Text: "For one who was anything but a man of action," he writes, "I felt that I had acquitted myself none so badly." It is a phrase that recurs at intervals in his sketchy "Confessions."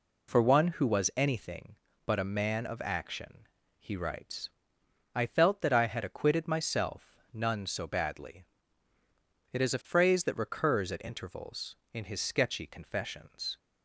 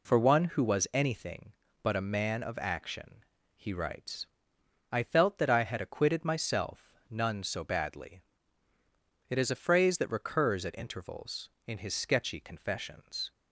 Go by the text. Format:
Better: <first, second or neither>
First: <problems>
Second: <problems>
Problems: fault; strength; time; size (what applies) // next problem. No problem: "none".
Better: neither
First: pauses between "myself" and "none"; slight; at 7.1 s; 0.16 s long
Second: pauses between "myself" and "none"; slight; at 6.9 s; 0.16 s long